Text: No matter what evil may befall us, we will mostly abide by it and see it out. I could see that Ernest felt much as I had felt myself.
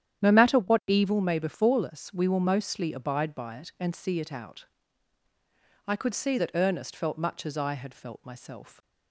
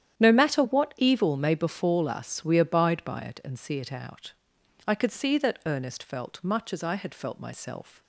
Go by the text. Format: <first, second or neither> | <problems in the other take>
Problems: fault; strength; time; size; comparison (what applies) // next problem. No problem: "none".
first | starts louder than the rest; strong; until 1.2 s; 10 dB; strong in the first // skips "will mostly"; at 2.5 s